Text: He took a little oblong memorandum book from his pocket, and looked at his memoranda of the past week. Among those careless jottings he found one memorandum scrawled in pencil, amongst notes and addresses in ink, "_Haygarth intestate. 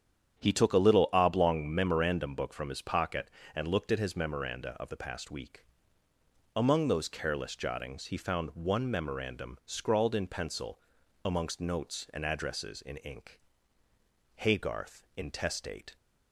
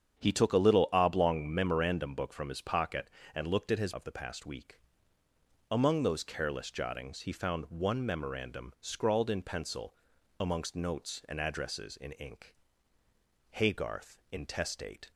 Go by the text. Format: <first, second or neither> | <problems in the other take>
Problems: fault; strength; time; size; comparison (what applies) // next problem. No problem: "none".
first | starts louder than the rest; strong; until 1.2 s; 8 dB; strong in the first // skips "memoranda"; at 3.9 s